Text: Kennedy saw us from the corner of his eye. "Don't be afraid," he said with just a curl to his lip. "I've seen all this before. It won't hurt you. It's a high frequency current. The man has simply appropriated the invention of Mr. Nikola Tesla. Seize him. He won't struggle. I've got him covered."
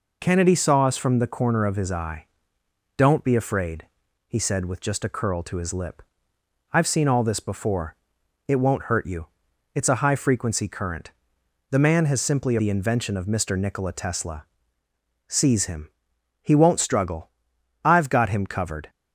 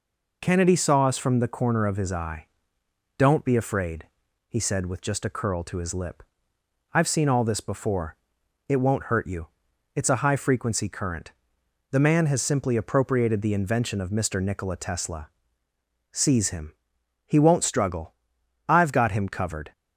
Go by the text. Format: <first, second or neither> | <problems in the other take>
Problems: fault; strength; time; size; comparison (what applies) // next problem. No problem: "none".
second | skips "appropriated"; at 12.5 s